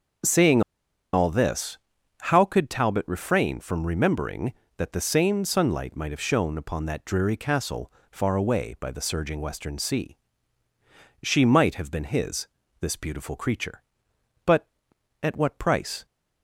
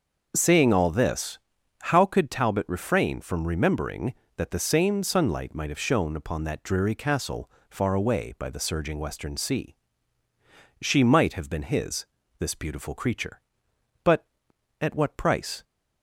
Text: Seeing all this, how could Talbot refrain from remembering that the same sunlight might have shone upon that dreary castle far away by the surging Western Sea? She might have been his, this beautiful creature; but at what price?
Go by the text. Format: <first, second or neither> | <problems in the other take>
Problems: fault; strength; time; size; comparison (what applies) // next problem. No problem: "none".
second | starts louder than the rest; noticeable; until 1.7 s; 6 dB; also in the second // pauses between "Seeing" and "all"; noticeable; at 0.6 s; 0.52 s long // pauses between "castle" and "far"; slight; at 7.9 s; 0.20 s long; slight in the second